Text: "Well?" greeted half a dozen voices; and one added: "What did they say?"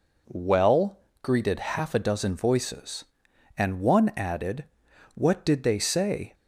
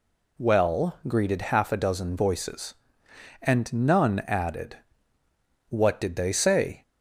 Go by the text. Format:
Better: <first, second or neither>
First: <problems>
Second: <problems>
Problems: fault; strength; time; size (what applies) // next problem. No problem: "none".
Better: first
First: none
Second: says "none" for "one"; at 3.7 s